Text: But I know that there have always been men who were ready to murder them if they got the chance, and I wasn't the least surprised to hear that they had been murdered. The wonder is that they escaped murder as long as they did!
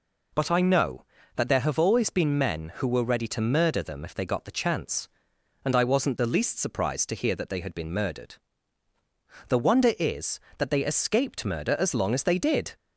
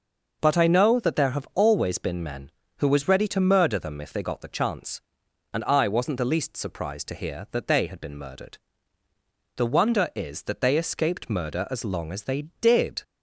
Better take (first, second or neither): first